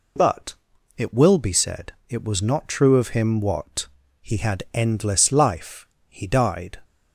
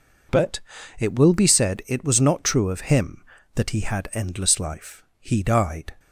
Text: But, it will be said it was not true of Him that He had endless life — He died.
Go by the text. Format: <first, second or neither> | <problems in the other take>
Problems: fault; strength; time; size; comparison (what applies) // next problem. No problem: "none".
second | pauses between "said" and "it"; slight; at 1.9 s; 0.16 s long // says "what" for "that"; at 3.3 s